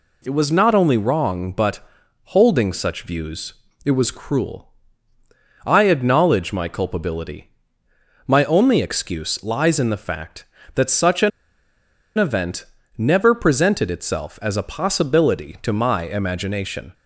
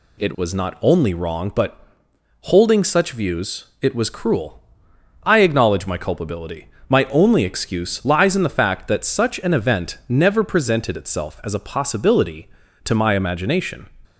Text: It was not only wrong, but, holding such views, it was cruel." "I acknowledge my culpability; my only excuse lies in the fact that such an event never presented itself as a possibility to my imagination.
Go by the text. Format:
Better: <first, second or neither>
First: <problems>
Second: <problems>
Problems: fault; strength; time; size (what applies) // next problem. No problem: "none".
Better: second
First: pauses between "an" and "event"; noticeable; at 11.3 s; 0.88 s long // pauses between "event" and "never"; slight; at 12.6 s; 0.34 s long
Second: none